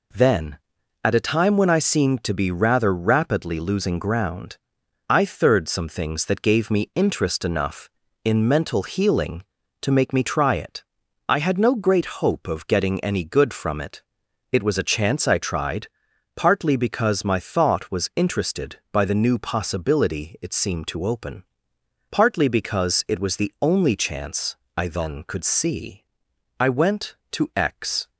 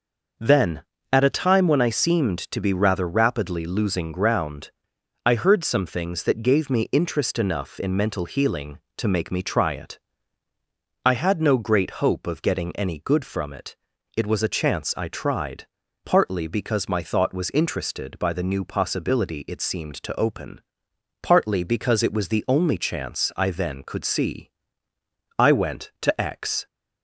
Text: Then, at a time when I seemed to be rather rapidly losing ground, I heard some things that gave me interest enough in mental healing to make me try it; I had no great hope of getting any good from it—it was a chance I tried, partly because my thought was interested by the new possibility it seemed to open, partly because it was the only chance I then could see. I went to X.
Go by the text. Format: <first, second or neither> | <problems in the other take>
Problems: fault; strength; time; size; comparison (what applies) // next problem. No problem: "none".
second | says "third" for "heard"; at 5.2 s // pauses between "chance" and "I"; slight; at 24.5 s; 0.18 s long